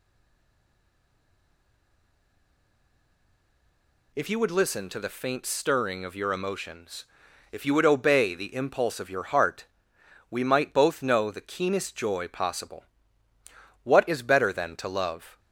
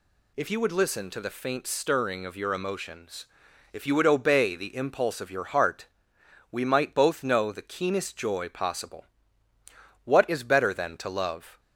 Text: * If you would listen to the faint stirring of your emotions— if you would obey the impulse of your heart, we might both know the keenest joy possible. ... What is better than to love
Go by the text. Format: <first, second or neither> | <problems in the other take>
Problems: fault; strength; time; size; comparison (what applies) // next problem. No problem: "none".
second | stays silent before the first word; strong; until 4.1 s; 4.1 s long